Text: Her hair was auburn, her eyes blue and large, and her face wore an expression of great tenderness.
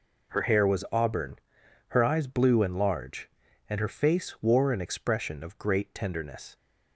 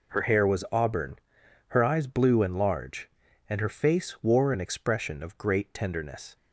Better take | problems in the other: neither | none

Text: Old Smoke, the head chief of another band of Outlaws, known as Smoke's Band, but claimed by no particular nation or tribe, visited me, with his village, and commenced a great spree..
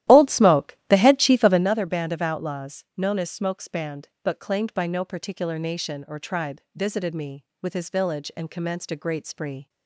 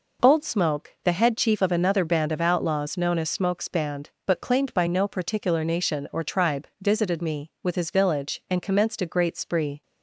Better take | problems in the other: second | starts louder than the rest; strong; until 1.7 s; 13.5 dB

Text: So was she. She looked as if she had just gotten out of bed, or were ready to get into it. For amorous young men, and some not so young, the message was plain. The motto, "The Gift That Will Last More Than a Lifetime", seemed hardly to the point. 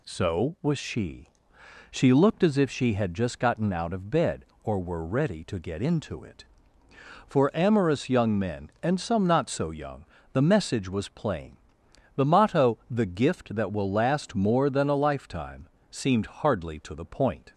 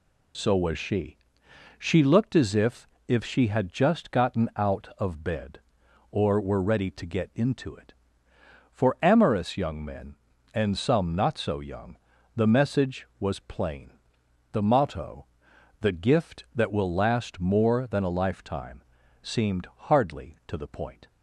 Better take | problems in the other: first | says "if" twice; at 3.0 s

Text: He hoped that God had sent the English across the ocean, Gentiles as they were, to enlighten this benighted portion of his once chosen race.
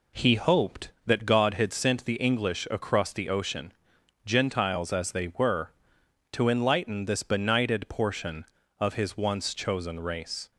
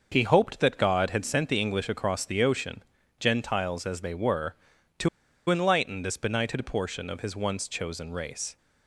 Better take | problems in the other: first | starts louder than the rest; noticeable; until 1.1 s; 6 dB // pauses between "to" and "enlighten"; at 5.0 s; 0.40 s long

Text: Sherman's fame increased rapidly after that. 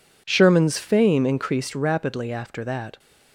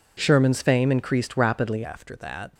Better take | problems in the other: first | changes voice at "after"; from 1.8 s on; 0.7 s long

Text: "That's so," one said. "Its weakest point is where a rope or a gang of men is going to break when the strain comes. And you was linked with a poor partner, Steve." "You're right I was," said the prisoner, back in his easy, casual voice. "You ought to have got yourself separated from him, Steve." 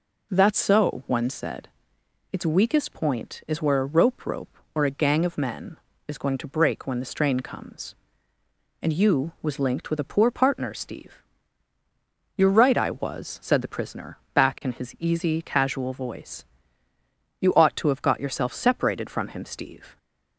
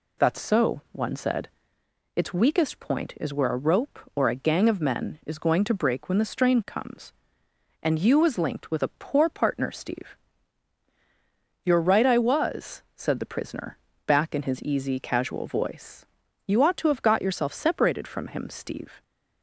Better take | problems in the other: second | says "rope" twice; at 4.2 s

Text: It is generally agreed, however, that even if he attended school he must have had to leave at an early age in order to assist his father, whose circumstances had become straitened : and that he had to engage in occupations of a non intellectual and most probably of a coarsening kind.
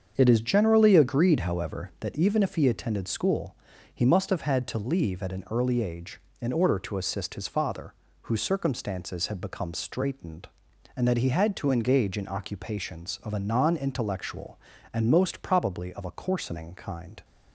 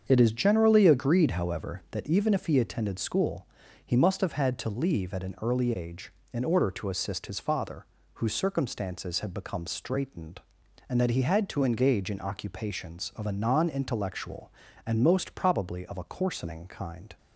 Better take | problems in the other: neither | starts louder than the rest; the same in both // pauses between "school" and "he"; the same in both

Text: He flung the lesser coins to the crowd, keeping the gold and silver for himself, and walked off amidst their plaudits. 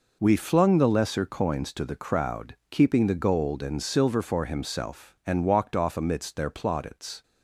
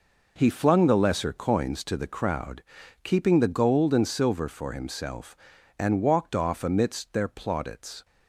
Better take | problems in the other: second | says "We" for "He"; at 0.2 s

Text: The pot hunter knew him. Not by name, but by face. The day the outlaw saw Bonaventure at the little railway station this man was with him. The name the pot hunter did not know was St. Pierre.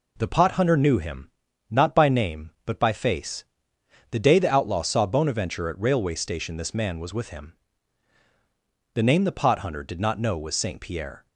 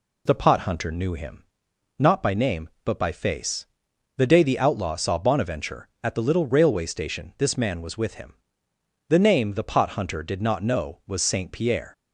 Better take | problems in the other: second | skips "the little"; at 5.7 s

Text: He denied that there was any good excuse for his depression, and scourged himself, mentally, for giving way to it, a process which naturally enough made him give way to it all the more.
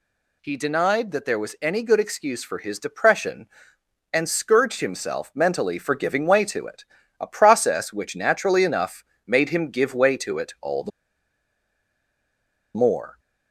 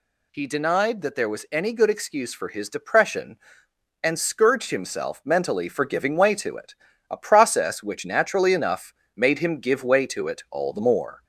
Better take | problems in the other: second | pauses between "enough" and "made"; slight; at 9.0 s; 0.22 s long; slight in the second // pauses between "the" and "more"; strong; at 10.9 s; 1.8 s long

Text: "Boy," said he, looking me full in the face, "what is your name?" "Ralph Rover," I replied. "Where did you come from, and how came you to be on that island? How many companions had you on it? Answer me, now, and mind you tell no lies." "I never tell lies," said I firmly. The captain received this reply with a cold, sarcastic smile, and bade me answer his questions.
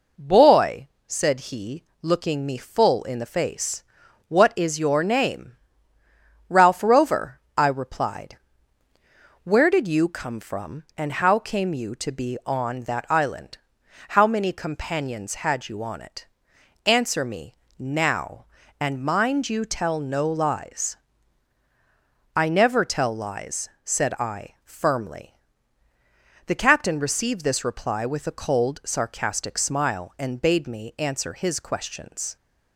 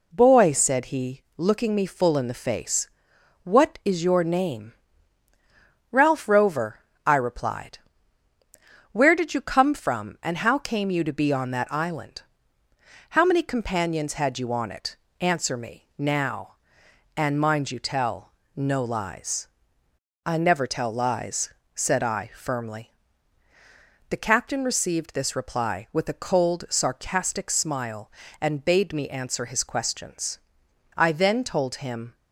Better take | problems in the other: first | pauses between "tell" and "no"; slight; at 18.3 s; 0.22 s long // goes on to say "I then told him"; noticeable; from 30.9 s on; 1.1 s long

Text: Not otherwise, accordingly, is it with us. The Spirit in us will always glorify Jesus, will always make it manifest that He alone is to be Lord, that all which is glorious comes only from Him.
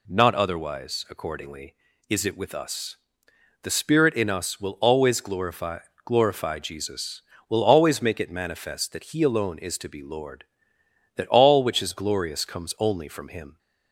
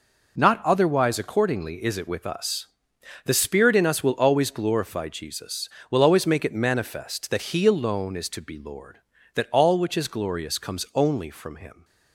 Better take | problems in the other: second | says "glorify" twice; at 6.0 s

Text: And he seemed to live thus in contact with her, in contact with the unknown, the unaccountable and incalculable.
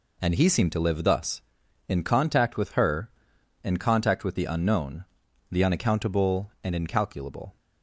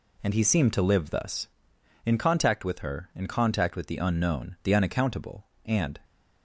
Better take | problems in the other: first | stops before "incalculable"; at 6.0 s

